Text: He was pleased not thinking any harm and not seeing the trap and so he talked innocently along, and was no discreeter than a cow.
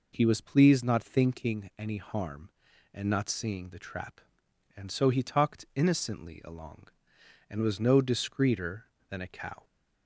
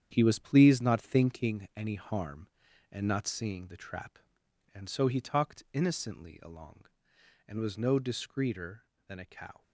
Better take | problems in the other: first | gets quieter; strong; throughout; 8.5 dB

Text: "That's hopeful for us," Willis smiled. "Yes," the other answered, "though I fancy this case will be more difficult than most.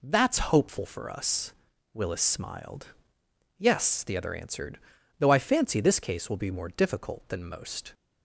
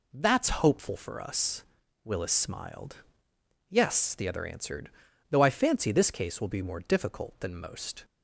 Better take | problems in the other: neither | none

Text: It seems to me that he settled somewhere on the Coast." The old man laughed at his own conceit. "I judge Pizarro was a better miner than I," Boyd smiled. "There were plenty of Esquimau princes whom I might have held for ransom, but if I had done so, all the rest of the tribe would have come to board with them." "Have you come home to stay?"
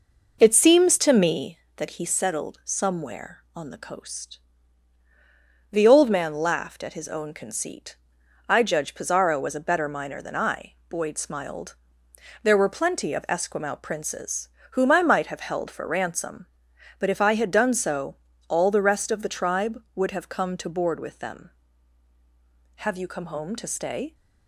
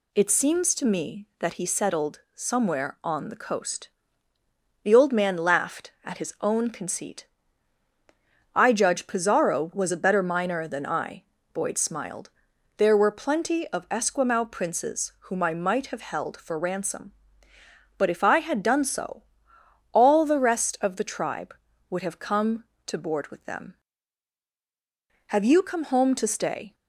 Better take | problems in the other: second | starts louder than the rest; noticeable; until 1.5 s; 5 dB // pauses between "princes" and "whom"; slight; at 14.4 s; 0.26 s long; slight in the second

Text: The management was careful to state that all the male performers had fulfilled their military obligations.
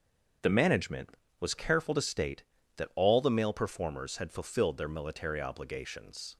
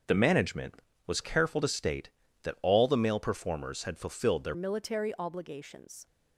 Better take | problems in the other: first | starts louder than the rest; until 1.3 s; 6.5 dB; also in the first // changes voice at "military"; from 4.5 s on; 1.5 s long

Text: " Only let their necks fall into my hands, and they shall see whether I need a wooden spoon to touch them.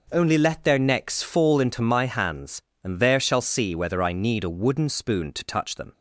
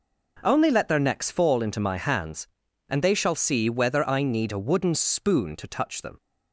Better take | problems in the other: second | says "there" for "they"; at 2.9 s

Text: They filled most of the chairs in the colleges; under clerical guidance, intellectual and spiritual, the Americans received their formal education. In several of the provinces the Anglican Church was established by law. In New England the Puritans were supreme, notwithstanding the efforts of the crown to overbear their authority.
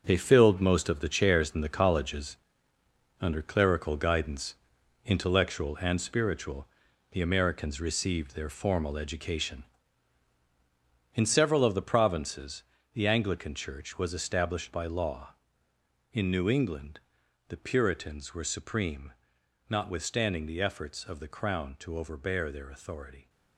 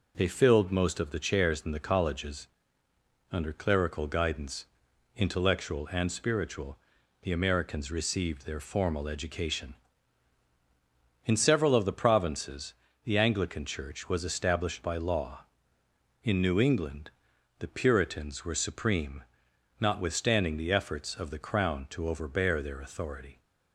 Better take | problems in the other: second | gets quieter; strong; throughout; 9.5 dB // pauses between "provinces" and "the"; slight; at 12.6 s; 0.32 s long; slight in the second // pauses between "England" and "the"; noticeable; at 16.9 s; 0.48 s long; noticeable in the second

